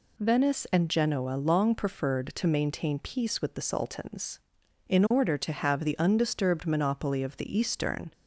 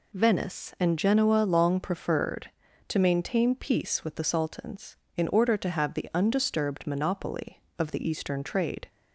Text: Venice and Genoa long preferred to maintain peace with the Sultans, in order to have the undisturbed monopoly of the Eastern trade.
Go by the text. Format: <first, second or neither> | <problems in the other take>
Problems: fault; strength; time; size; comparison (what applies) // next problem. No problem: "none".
second | stops before "trade"; at 8.1 s